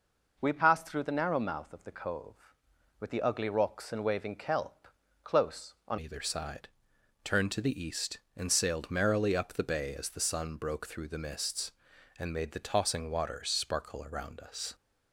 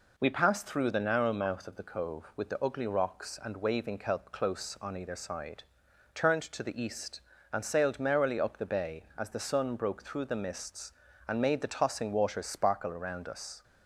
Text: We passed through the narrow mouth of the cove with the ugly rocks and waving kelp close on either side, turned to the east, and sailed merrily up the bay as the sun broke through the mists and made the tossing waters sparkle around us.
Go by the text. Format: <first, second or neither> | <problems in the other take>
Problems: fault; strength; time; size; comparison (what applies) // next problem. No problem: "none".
second | pauses between "kelp" and "close"; slight; at 4.8 s; 0.36 s long // changes voice at "either"; from 5.9 s on; 8.8 s long